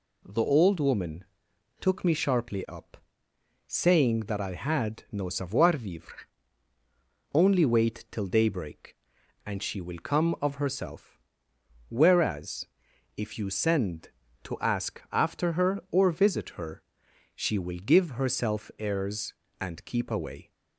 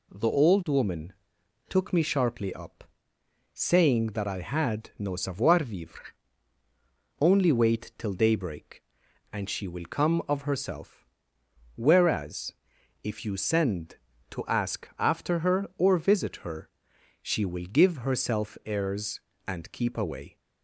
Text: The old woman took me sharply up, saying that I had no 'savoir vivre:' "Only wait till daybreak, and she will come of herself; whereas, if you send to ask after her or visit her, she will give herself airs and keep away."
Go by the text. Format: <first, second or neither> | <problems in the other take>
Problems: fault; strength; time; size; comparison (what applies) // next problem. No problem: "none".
neither | pauses between "woman" and "took"; noticeable; the same in both